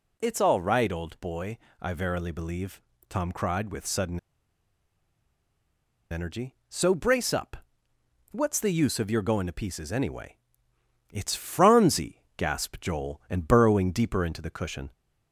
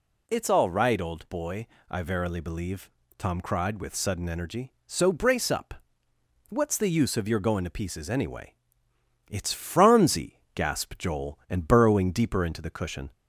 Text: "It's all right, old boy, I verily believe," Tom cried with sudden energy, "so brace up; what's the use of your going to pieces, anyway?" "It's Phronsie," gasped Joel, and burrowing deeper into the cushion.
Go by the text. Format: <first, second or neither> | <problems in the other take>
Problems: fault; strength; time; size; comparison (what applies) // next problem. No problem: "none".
second | pauses between "sudden" and "energy"; strong; at 4.1 s; 1.9 s long